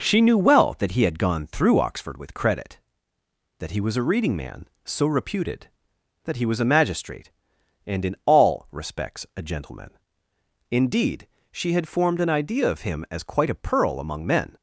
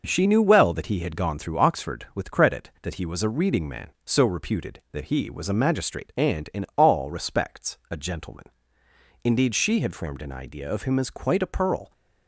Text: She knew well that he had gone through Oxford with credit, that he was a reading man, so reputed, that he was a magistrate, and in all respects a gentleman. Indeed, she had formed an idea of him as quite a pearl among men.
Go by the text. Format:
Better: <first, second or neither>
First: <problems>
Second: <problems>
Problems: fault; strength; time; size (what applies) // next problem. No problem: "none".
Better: first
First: none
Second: stops before "among men"; at 11.9 s